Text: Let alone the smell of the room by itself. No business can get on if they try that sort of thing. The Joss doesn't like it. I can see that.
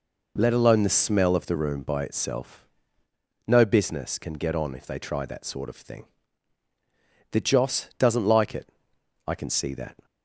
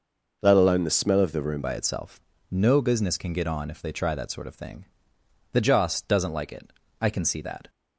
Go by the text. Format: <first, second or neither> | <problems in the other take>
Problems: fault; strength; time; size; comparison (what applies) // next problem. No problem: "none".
first | changes voice at "by"; from 1.6 s on; 6.0 s long